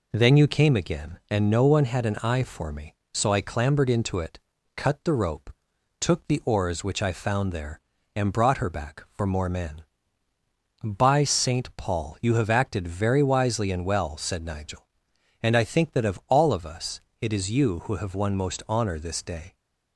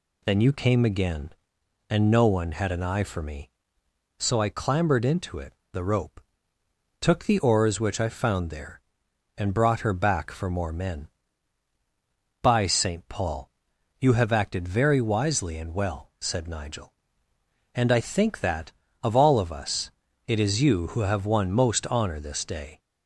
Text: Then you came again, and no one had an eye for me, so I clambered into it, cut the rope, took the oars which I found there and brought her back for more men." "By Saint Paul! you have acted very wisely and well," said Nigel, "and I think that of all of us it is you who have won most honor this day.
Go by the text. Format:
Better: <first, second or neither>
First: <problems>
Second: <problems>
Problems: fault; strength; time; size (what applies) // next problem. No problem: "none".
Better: first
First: pauses between "us" and "it"; slight; at 16.9 s; 0.22 s long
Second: skips "cut"; at 5.6 s // pauses between "us" and "it"; slight; at 19.9 s; 0.36 s long